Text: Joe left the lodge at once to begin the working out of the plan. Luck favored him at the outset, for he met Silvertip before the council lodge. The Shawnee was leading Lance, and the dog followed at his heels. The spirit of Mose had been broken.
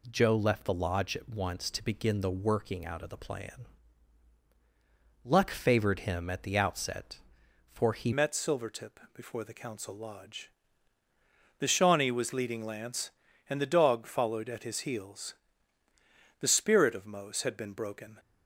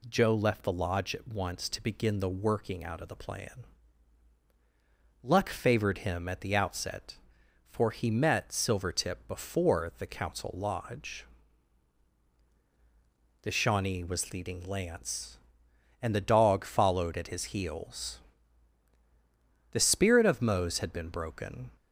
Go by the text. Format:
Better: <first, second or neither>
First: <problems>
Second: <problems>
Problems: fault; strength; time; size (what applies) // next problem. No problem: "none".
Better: second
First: changes voice at "met"; from 8.1 s on; 10.0 s long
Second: none